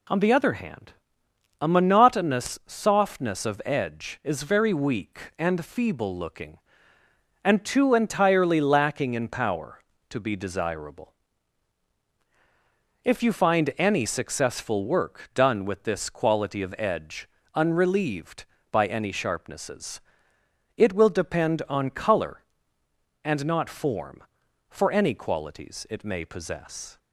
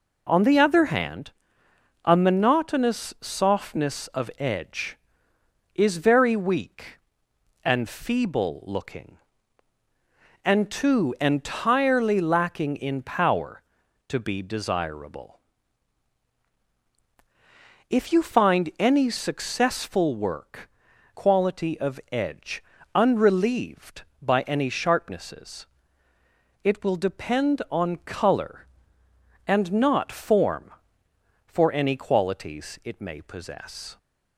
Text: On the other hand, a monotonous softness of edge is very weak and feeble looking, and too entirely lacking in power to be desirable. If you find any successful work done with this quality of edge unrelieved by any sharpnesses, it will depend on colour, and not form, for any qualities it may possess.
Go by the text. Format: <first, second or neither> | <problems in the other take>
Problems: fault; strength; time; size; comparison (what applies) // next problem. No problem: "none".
first | skips "done with this"; at 20.9 s // pauses between "edge" and "unrelieved"; slight; at 22.6 s; 0.32 s long; slight in the first